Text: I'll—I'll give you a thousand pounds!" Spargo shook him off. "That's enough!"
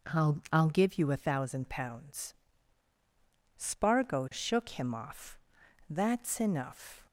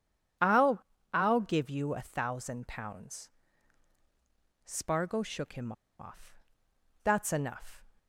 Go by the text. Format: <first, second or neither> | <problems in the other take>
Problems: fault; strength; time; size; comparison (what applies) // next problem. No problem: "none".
first | pauses between "him" and "off"; slight; at 5.7 s; 0.27 s long